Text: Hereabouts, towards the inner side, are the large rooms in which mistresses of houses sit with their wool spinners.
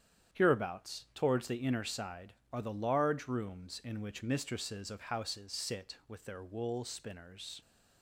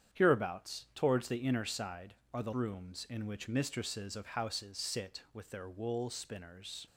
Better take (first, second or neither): first